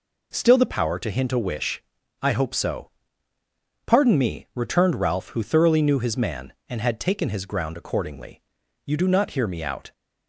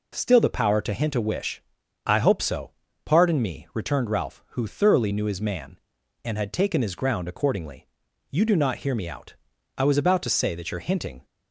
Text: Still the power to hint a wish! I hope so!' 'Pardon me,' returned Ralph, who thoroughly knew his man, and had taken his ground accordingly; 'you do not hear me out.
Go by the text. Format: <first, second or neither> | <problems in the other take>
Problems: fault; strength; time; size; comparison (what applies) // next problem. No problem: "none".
first | goes on to say "I was about to say that your hinting"; from 9.7 s on; 1.5 s long